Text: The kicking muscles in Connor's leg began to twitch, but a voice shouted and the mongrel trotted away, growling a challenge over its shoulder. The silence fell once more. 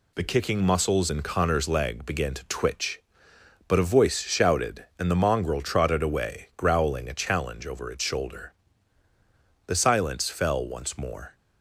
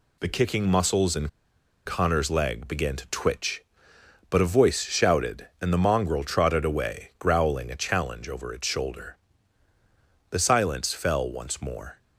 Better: first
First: none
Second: pauses between "in" and "Connor's"; noticeable; at 1.2 s; 0.58 s long

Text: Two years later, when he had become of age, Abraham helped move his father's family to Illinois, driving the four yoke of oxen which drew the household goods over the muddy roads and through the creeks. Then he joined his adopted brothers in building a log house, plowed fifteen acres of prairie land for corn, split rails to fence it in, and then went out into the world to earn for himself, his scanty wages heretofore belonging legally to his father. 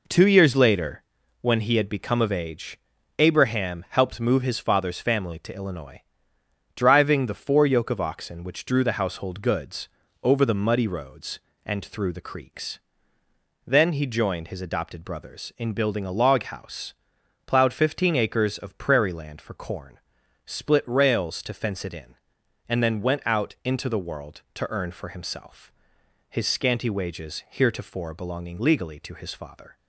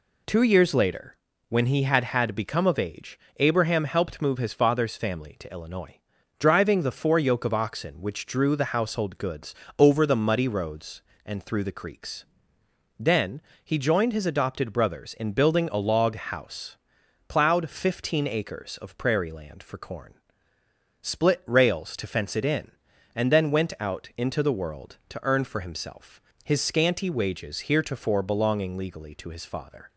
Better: first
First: pauses between "goods" and "over"; slight; at 9.8 s; 0.32 s long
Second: says "had" twice; at 2.0 s // pauses between "goods" and "over"; slight; at 9.5 s; 0.24 s long // pauses between "Then" and "he"; slight; at 13.4 s; 0.22 s long

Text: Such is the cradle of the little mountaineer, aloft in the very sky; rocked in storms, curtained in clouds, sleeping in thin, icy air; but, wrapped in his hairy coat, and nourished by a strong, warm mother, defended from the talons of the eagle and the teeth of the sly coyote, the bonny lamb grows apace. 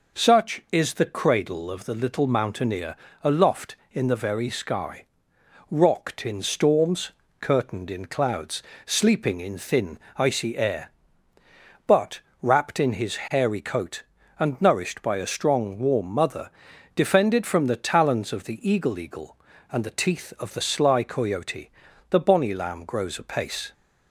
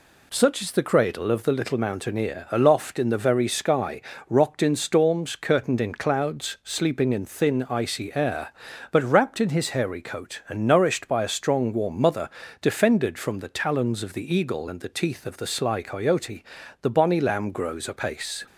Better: second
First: says "eagle" twice; at 18.9 s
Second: none

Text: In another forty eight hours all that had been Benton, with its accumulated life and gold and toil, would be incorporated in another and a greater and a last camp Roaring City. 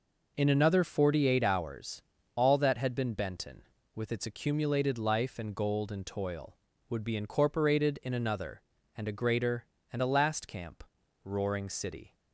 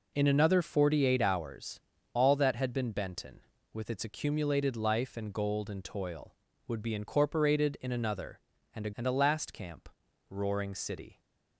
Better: first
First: pauses between "hours" and "all"; slight; at 2.0 s; 0.32 s long // pauses between "camp" and "Roaring"; at 10.8 s; 0.42 s long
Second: pauses between "hours" and "all"; slight; at 1.8 s; 0.32 s long // skips "greater"; at 8.9 s // pauses between "camp" and "Roaring"; at 9.8 s; 0.42 s long

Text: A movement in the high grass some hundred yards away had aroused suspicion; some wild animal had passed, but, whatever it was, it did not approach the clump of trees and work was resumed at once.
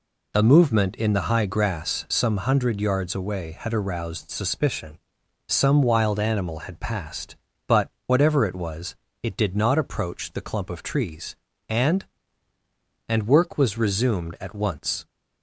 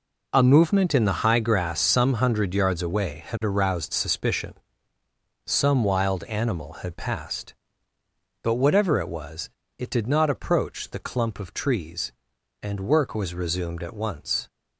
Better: second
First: says "and" twice; at 13.0 s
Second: none

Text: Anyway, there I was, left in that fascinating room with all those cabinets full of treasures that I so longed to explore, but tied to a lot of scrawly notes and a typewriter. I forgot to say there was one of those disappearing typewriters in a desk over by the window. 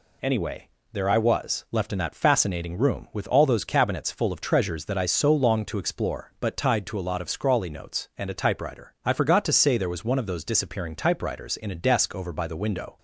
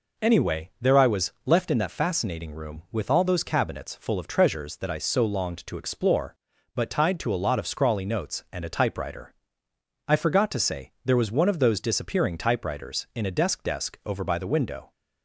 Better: first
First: none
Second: says "desk" twice; at 13.6 s

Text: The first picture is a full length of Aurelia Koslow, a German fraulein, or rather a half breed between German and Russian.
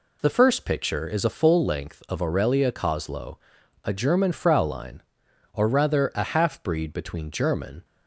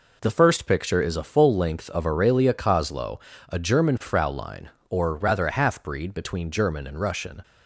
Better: second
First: stops before "and Russian"; at 7.8 s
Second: none

